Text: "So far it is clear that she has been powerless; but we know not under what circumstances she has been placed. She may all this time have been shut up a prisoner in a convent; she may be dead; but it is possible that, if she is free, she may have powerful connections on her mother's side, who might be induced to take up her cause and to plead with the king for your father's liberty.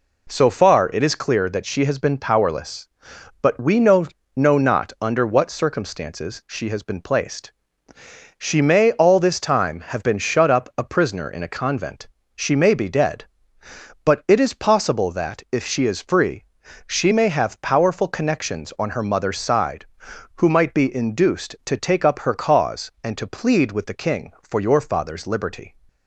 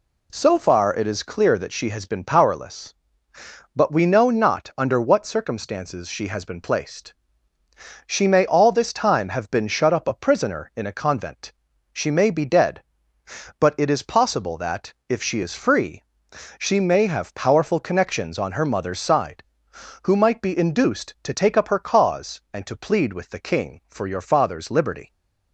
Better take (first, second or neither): second